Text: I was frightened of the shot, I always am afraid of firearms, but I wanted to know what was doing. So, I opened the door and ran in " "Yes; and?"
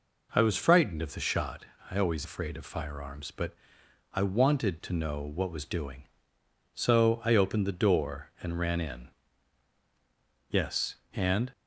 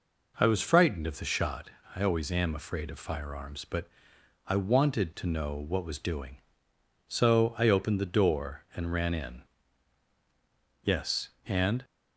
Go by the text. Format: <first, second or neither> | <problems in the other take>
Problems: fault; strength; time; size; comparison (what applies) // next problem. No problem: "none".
second | skips "am"; at 2.2 s // pauses between "but" and "I"; noticeable; at 3.5 s; 0.60 s long; noticeable in the second